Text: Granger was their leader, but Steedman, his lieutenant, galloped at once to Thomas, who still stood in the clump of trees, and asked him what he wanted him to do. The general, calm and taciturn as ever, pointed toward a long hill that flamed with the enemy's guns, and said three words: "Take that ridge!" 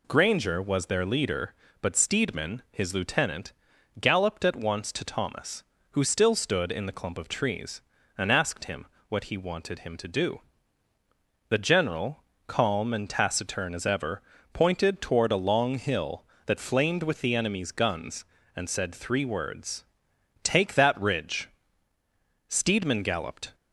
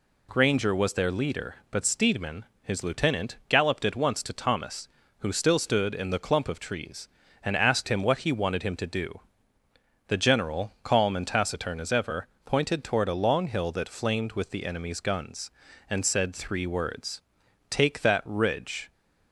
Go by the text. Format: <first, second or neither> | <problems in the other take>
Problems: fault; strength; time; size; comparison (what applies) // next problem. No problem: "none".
second | pauses between "him" and "what"; slight; at 8.8 s; 0.22 s long // goes on to say "Steedman galloped"; noticeable; from 22.4 s on; 1.0 s long